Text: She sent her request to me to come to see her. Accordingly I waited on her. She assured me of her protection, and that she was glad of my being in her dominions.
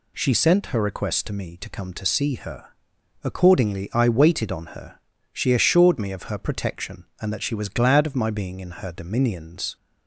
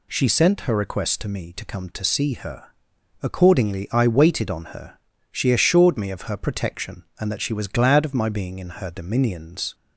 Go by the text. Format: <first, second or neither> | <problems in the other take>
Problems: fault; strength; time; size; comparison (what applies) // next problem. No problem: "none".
neither | none